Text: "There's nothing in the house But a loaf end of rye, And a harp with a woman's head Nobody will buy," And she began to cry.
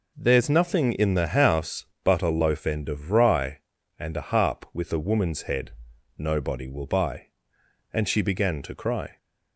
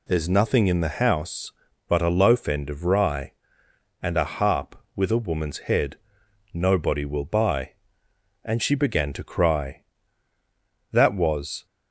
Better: first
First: pauses between "head" and "Nobody"; noticeable; at 5.7 s; 0.46 s long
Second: pauses between "head" and "Nobody"; noticeable; at 5.9 s; 0.56 s long // goes on to say "That was"; noticeable; from 10.9 s on; 0.74 s long

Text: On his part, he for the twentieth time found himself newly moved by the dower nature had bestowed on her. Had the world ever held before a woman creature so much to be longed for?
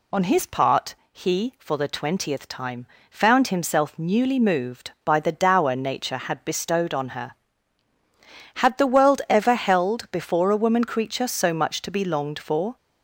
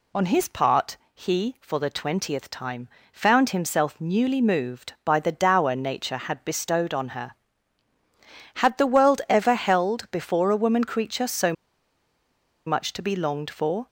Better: first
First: pauses between "time" and "found"; slight; at 2.8 s; 0.24 s long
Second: pauses between "time" and "found"; slight; at 2.8 s; 0.24 s long // pauses between "so" and "much"; at 11.5 s; 1.1 s long

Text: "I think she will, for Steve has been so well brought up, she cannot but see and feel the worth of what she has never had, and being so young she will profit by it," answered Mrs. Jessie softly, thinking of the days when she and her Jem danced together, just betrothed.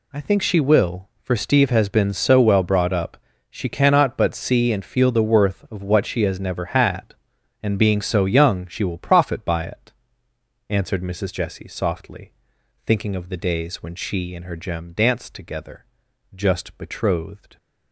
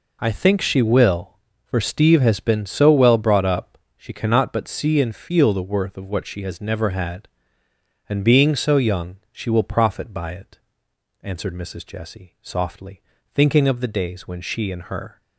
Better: first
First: none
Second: stops before "Jem danced together just betrothed"; at 15.2 s

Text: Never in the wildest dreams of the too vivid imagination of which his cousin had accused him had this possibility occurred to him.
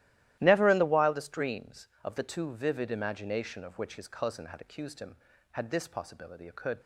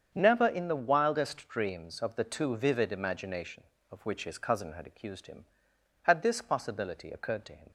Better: second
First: starts louder than the rest; strong; until 1.4 s; 14.5 dB // stops before "to him"; at 6.8 s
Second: starts louder than the rest; strong; until 1.1 s; 7.5 dB

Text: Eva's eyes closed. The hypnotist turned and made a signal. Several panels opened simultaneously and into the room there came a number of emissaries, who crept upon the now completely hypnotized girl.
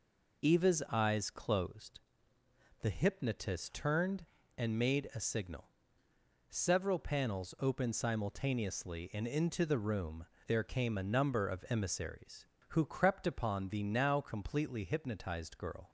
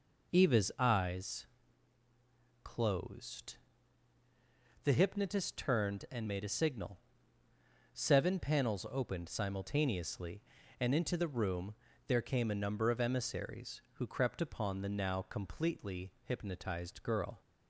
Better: first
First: pauses between "room" and "there"; slight; at 10.2 s; 0.20 s long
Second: pauses between "eyes" and "closed"; at 1.4 s; 1.1 s long // says "Seven" for "Several"; at 7.9 s // pauses between "room" and "there"; slight; at 11.7 s; 0.36 s long // pauses between "completely" and "hypnotized"; slight; at 16.1 s; 0.16 s long

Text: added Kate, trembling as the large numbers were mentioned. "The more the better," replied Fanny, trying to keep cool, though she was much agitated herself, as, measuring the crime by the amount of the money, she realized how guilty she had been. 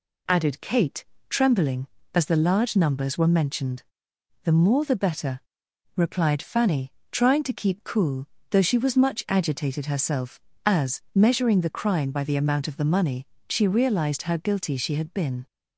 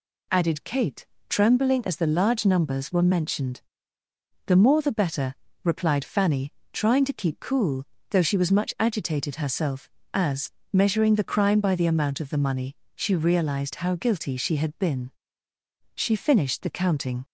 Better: first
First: none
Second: goes on to say "She finished the counting"; noticeable; from 15.9 s on; 1.3 s long

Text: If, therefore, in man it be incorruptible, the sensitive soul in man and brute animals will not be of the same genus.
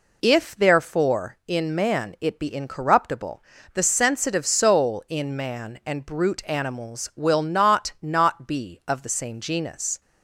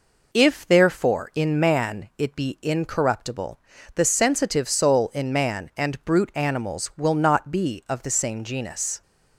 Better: second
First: says "not" twice; at 8.0 s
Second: none

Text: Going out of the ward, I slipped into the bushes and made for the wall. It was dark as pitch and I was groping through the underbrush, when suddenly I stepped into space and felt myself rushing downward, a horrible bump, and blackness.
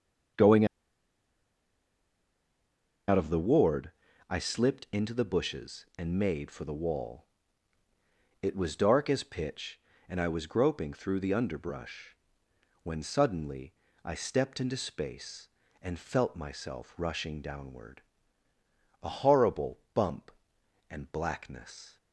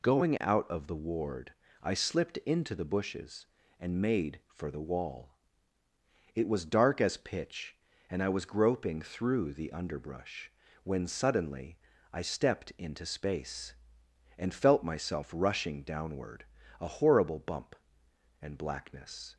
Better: second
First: starts louder than the rest; until 3.8 s; 7 dB // pauses between "Going" and "out"; strong; at 0.6 s; 2.4 s long // pauses between "suddenly" and "I"; slight; at 13.7 s; 0.30 s long // pauses between "horrible" and "bump"; slight; at 19.7 s; 0.16 s long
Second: pauses between "suddenly" and "I"; slight; at 11.7 s; 0.36 s long

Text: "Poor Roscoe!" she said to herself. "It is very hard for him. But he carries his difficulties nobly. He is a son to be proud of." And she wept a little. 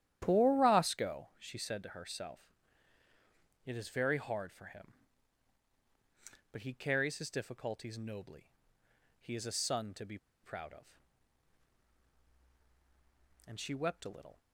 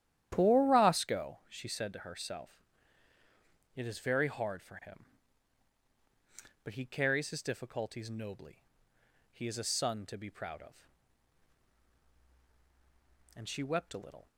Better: second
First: starts louder than the rest; strong; until 1.2 s; 11.5 dB // pauses between "be" and "proud"; slight; at 10.1 s; 0.25 s long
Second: starts louder than the rest; strong; until 1.3 s; 11.5 dB

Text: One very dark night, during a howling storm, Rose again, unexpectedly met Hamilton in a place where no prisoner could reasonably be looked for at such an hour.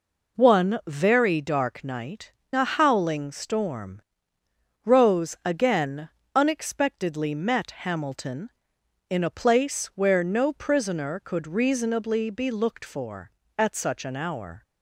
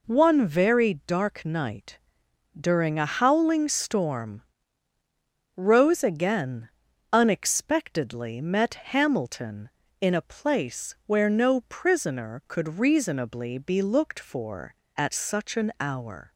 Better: second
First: skips "during"; at 2.4 s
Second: none

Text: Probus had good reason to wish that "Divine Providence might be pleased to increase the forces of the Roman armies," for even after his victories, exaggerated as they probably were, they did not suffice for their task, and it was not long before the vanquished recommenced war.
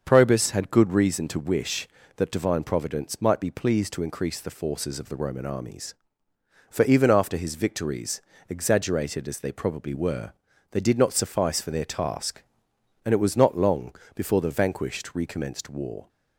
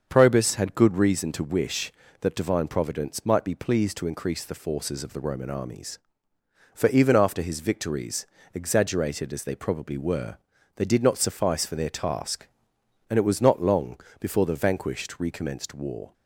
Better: neither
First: starts louder than the rest; until 1.0 s; 6.5 dB // pauses between "long" and "before"; slight; at 13.9 s; 0.20 s long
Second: starts louder than the rest; until 1.1 s; 7 dB // pauses between "long" and "before"; slight; at 13.9 s; 0.20 s long

